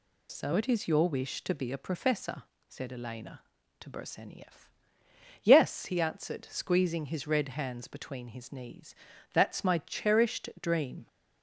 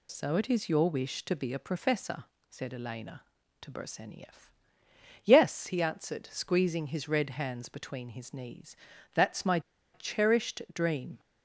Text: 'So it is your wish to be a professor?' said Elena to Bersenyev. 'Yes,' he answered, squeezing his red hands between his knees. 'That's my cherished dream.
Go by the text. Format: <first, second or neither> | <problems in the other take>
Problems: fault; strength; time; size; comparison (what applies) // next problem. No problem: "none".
first | pauses between "my" and "cherished"; slight; at 9.6 s; 0.33 s long